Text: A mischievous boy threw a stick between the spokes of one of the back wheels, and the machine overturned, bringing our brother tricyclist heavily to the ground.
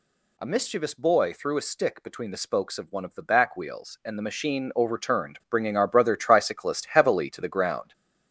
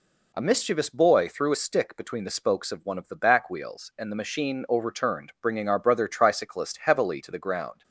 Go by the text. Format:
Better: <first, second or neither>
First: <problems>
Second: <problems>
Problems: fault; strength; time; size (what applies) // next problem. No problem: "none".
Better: second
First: gets louder; throughout; 6.5 dB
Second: none